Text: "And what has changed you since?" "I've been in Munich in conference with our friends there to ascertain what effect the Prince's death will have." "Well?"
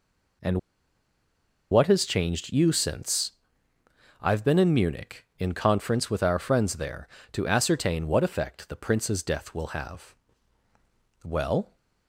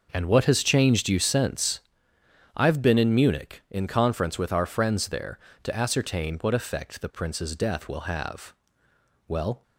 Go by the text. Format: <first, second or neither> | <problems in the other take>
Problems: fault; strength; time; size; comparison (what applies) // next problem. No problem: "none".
second | pauses between "And" and "what"; at 0.5 s; 1.1 s long